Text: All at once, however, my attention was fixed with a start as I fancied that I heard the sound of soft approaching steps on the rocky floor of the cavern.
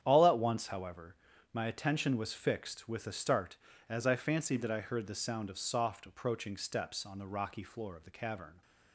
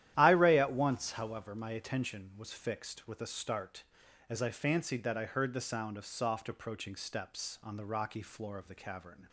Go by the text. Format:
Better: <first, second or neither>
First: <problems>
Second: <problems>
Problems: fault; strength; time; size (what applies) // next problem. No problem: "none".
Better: first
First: starts louder than the rest; strong; until 1.0 s; 9.5 dB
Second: starts louder than the rest; strong; until 1.1 s; 12 dB // says "Iray" for "All"; at 0.1 s